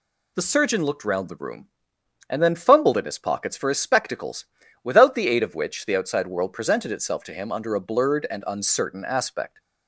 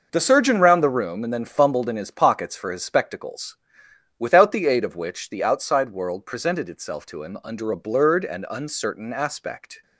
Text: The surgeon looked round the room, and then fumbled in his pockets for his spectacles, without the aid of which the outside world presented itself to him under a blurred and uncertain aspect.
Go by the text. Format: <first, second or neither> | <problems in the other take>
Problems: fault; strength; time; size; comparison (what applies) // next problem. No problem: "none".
first | skips "looked"; at 0.5 s